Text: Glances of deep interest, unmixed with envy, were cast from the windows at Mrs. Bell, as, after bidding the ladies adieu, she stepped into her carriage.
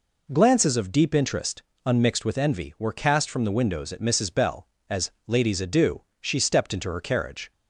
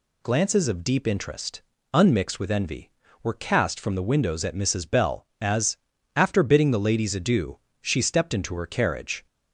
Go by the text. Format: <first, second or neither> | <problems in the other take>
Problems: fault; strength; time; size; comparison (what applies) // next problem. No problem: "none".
second | skips "after bidding the"; at 5.1 s